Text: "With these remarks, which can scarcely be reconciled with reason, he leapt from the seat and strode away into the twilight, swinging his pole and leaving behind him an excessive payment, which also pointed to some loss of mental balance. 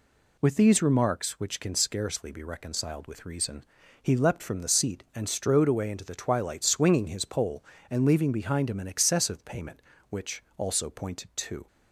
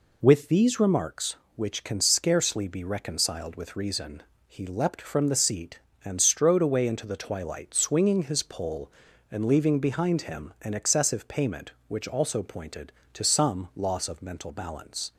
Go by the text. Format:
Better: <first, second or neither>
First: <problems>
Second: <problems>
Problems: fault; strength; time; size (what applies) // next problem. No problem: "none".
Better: second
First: stops before "some loss of mental balance"; at 11.6 s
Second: none